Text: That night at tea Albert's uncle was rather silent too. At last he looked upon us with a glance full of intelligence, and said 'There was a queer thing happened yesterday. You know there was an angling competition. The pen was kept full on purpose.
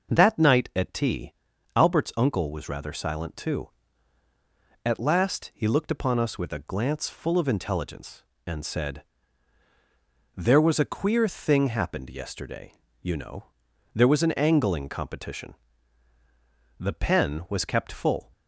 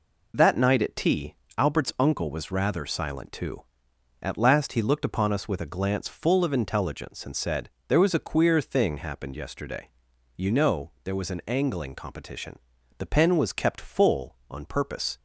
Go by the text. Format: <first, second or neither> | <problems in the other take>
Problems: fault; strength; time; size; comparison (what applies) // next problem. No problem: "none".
second | starts louder than the rest; noticeable; until 1.1 s; 6 dB // pauses between "tea" and "Albert's"; at 1.3 s; 0.42 s long; slight in the second // pauses between "said" and "There"; strong; at 9.0 s; 1.3 s long; slight in the second // pauses between "know" and "there"; noticeable; at 13.4 s; 0.50 s long // stops before "on purpose"; at 18.3 s